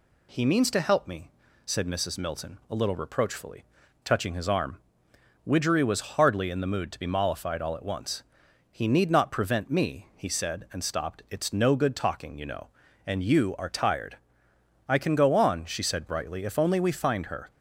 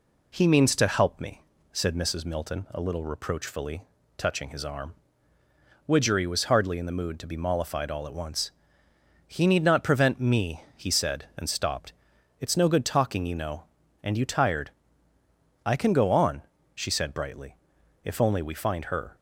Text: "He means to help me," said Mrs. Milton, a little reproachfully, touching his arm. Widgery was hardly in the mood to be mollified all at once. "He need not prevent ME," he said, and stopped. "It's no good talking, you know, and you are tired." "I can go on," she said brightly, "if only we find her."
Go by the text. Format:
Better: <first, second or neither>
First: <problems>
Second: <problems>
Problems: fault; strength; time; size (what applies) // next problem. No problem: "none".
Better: first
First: none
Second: skips "are"; at 14.2 s